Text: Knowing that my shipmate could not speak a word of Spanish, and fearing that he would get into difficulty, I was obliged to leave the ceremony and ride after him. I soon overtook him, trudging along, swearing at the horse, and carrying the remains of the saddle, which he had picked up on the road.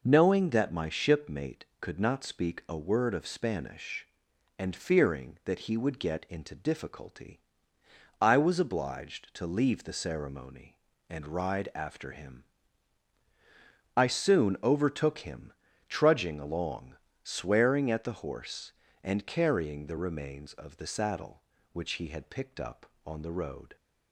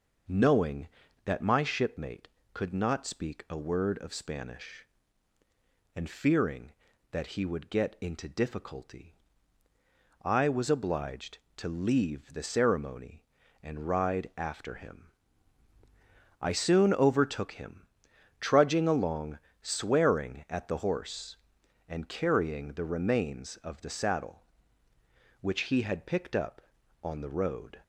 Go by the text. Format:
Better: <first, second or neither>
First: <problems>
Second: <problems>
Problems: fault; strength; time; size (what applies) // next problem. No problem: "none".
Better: neither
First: none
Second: none